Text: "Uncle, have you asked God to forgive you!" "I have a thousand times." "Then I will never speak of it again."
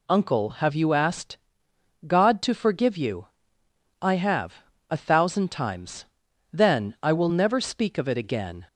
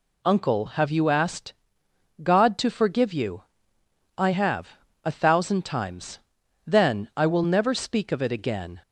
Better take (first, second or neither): neither